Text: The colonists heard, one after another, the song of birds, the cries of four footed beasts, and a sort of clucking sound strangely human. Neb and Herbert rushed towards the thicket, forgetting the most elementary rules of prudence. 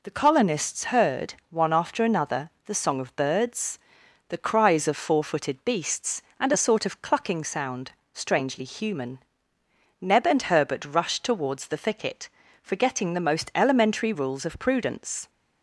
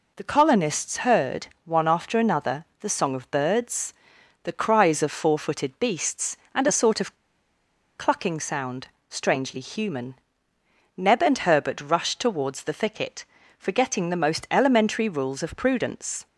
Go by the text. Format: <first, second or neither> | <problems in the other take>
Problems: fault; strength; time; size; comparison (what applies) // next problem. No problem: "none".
first | pauses between "of" and "clucking"; noticeable; at 7.1 s; 0.81 s long // pauses between "sound" and "strangely"; slight; at 8.8 s; 0.20 s long; slight in the first